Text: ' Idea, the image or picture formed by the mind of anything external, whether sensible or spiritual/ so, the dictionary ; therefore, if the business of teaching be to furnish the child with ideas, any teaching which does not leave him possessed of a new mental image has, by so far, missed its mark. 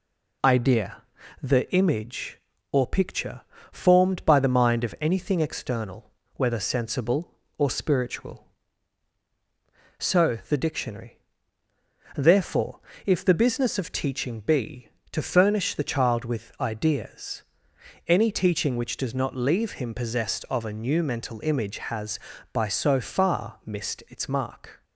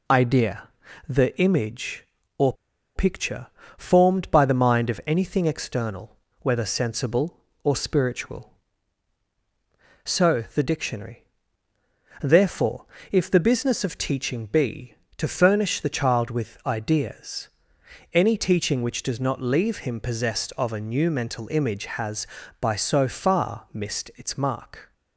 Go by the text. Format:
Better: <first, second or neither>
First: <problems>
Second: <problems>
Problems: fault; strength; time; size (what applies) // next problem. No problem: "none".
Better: first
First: pauses between "picture" and "formed"; slight; at 3.4 s; 0.30 s long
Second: pauses between "or" and "picture"; at 2.5 s; 0.42 s long // pauses between "picture" and "formed"; slight; at 3.4 s; 0.30 s long